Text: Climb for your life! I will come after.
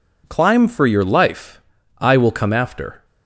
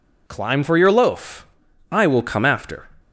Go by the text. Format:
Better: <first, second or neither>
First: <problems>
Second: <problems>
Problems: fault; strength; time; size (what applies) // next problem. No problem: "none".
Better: first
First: none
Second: says "loaf" for "life"; at 0.9 s